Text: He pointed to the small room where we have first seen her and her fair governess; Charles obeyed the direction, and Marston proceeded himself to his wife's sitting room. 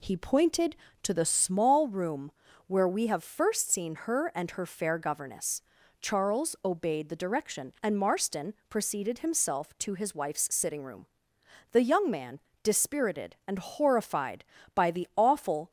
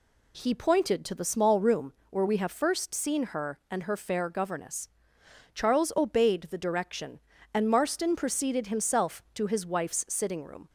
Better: second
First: pauses between "room" and "where"; slight; at 2.3 s; 0.36 s long // goes on to say "The young man dispirited and horrified by the awful"; strong; from 11.7 s on; 3.9 s long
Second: pauses between "room" and "where"; slight; at 1.9 s; 0.16 s long

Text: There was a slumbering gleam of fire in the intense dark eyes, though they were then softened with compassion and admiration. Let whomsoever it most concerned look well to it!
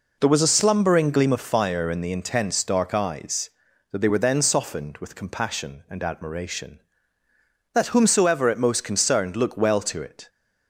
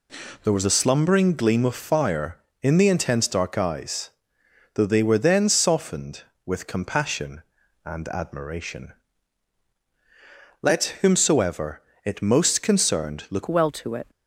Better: first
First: none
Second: pauses between "whomsoever" and "it"; slight; at 11.8 s; 0.24 s long // changes voice at "well"; from 13.4 s on; 0.6 s long

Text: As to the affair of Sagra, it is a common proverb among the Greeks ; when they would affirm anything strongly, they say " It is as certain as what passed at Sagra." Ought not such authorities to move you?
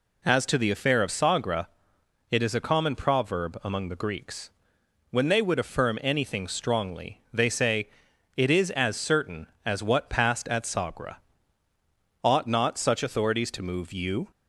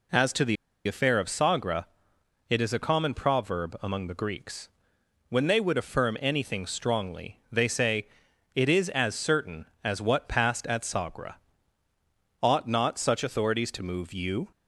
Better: first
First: none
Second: pauses between "the" and "affair"; slight; at 0.5 s; 0.31 s long

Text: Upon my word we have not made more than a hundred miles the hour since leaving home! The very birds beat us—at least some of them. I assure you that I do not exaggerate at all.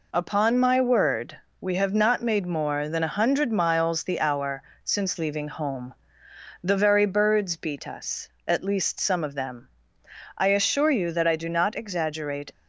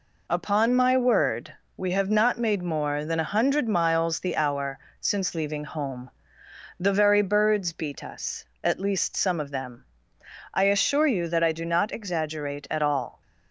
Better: second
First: pauses between "word" and "we"; slight; at 1.3 s; 0.22 s long // pauses between "hour" and "since"; slight; at 4.6 s; 0.22 s long // stops before "at all"; at 12.5 s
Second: pauses between "word" and "we"; slight; at 1.5 s; 0.22 s long // pauses between "hour" and "since"; slight; at 4.7 s; 0.22 s long

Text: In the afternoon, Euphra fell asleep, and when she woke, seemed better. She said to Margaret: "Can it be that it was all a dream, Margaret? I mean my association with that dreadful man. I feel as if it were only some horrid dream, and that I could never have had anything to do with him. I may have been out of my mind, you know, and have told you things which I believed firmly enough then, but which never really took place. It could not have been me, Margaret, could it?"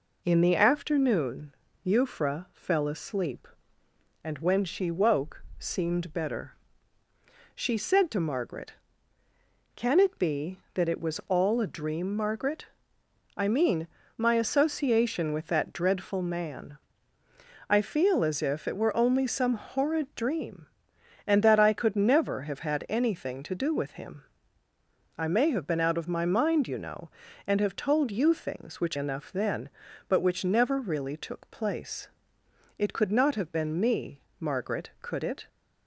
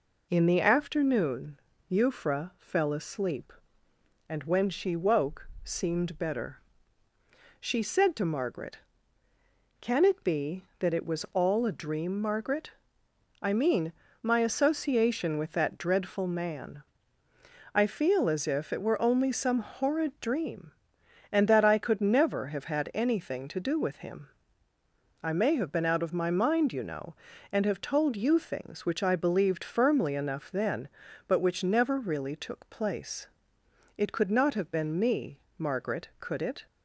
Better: second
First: pauses between "mean" and "my"; slight; at 13.8 s; 0.30 s long // skips "I believed firmly"; at 28.9 s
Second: pauses between "mean" and "my"; slight; at 13.9 s; 0.30 s long

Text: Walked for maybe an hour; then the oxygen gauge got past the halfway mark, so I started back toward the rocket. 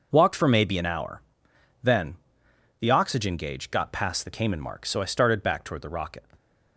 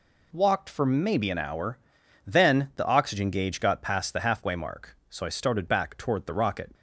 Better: second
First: pauses between "then" and "the"; noticeable; at 2.1 s; 0.64 s long // says "cayman" for "halfway"; at 4.3 s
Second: none

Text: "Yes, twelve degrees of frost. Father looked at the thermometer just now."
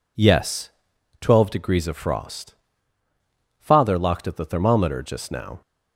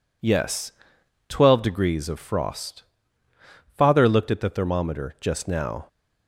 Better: second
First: says "locked" for "looked"; at 3.9 s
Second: none

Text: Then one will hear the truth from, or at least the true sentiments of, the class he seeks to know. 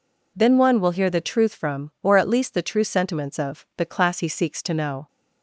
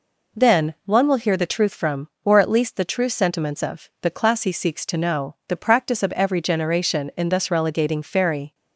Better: first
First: none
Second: goes on to say "The practice of every generation in thus relegating fairy"; strong; from 5.4 s on; 3.0 s long

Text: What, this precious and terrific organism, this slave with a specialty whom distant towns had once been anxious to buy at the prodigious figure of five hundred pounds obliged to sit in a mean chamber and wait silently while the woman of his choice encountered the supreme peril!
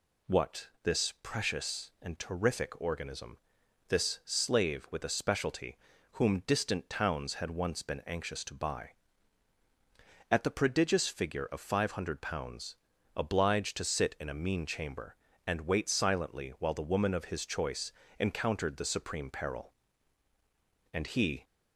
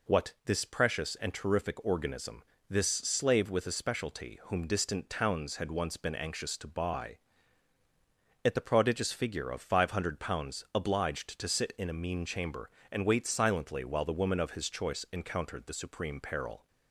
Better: second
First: pauses between "specialty" and "whom"; at 5.7 s; 0.38 s long // pauses between "pounds" and "obliged"; at 12.7 s; 0.40 s long // pauses between "choice" and "encountered"; slight; at 17.9 s; 0.26 s long // goes on to say "And he"; from 20.9 s on; 0.50 s long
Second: none

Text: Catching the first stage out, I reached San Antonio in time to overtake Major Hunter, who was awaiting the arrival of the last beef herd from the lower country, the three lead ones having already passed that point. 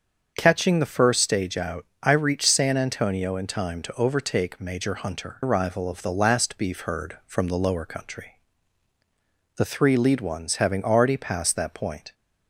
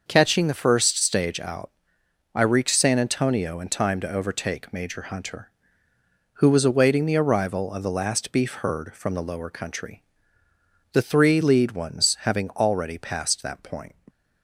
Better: second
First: starts louder than the rest; until 1.3 s; 7 dB // skips "who was awaiting the"; at 5.4 s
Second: starts louder than the rest; noticeable; until 1.0 s; 6 dB

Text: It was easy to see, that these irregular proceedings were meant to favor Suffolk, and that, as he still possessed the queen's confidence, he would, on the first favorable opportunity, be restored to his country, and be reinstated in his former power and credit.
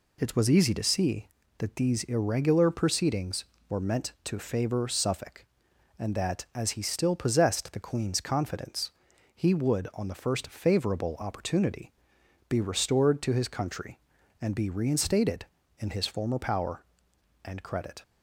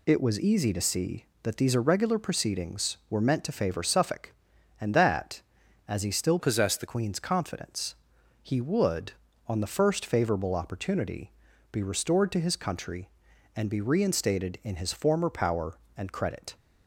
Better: first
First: none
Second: changes voice from "possessed" to "the"; from 6.3 to 6.8 s; 0.5 s long

